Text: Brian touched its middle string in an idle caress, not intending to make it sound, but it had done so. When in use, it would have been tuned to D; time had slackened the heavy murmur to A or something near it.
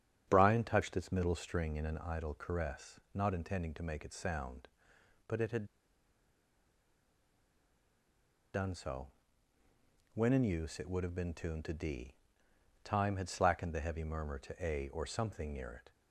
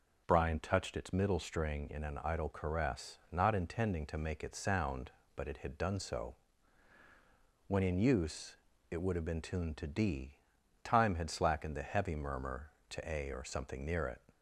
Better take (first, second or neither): second